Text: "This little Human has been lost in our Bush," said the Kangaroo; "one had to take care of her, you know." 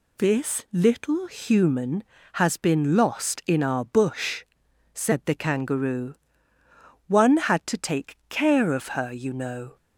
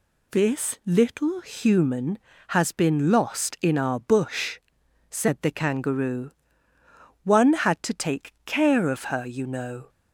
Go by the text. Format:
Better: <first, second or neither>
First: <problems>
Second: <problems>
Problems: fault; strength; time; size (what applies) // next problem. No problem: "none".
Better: neither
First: none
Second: none